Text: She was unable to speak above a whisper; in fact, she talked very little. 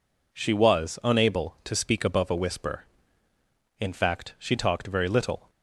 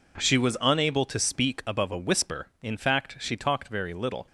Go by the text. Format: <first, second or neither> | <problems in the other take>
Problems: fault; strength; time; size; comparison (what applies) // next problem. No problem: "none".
neither | none